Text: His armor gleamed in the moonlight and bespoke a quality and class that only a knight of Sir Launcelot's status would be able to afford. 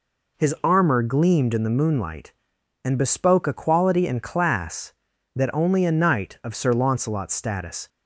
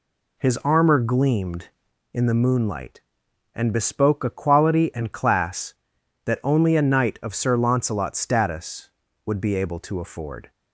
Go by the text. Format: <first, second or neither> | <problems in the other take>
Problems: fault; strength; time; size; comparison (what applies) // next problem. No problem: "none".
second | stops before "would be able to afford"; at 7.8 s